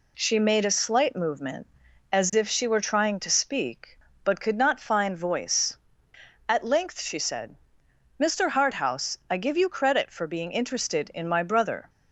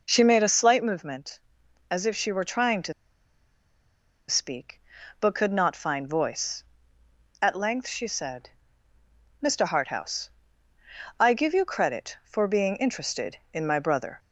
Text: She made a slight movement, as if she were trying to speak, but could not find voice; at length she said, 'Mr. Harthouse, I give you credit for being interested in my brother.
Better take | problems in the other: first | pauses between "to" and "speak"; strong; at 2.9 s; 1.3 s long

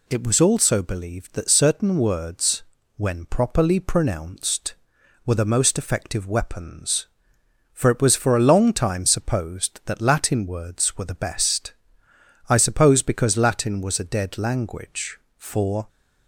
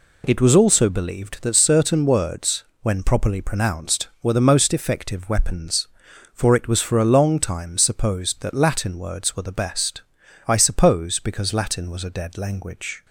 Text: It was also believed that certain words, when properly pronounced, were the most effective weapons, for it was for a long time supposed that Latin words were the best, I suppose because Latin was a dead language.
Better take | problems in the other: second | goes on to say "For"; from 15.3 s on; 0.52 s long

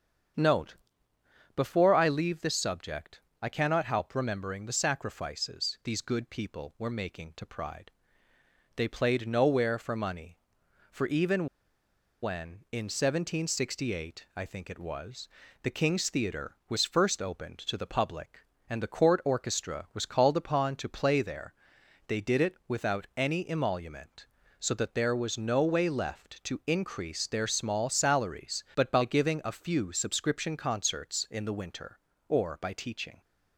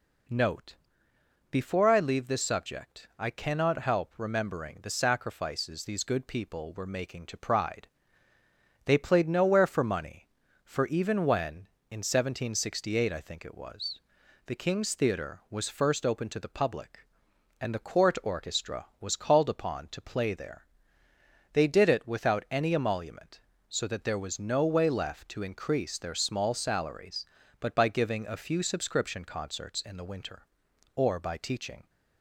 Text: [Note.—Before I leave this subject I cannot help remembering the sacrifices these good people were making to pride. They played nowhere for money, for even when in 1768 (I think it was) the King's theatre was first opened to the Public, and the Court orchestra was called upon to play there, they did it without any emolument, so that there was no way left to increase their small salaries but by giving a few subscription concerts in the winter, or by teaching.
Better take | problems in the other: second | starts louder than the rest; strong; until 2.1 s; 7.5 dB // pauses between "subject" and "I"; slight; at 3.2 s; 0.22 s long // pauses between "even" and "when"; noticeable; at 11.4 s; 0.76 s long

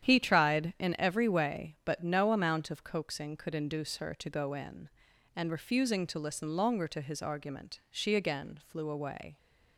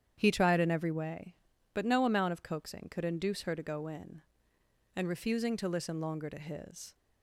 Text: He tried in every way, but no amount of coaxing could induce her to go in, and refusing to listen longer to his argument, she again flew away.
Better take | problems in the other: first | starts louder than the rest; strong; until 1.1 s; 9 dB; strong in the first // stops before "argument she again flew away"; at 6.9 s

